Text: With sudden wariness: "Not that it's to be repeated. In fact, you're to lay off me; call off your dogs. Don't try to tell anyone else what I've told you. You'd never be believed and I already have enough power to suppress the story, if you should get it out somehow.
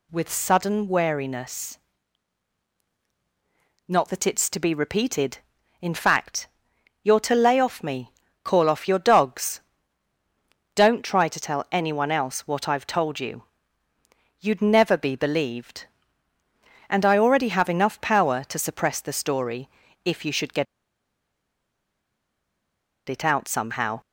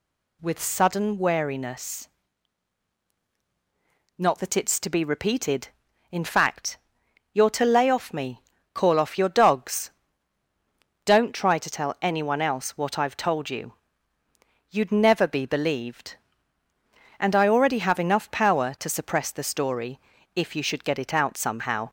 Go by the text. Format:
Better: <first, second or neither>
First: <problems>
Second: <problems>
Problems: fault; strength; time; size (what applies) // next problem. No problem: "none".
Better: second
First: pauses between "get" and "it"; strong; at 20.6 s; 2.4 s long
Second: none